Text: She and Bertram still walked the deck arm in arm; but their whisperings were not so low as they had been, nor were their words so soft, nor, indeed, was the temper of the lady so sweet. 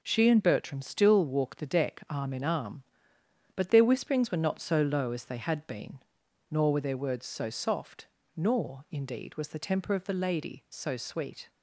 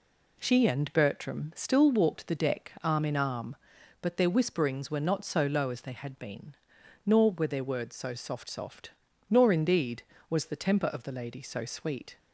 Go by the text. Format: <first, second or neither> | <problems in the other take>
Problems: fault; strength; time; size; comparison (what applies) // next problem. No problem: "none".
first | says "soft" twice; at 8.4 s